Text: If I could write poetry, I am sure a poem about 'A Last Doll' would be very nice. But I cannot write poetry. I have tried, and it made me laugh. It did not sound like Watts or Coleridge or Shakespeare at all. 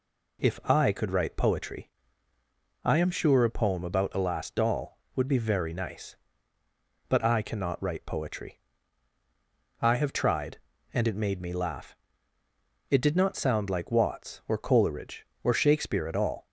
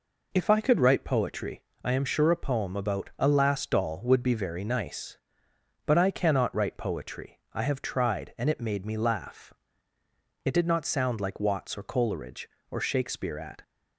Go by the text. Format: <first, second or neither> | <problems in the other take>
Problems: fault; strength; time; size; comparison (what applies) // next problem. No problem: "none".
first | stops before "all"; at 13.6 s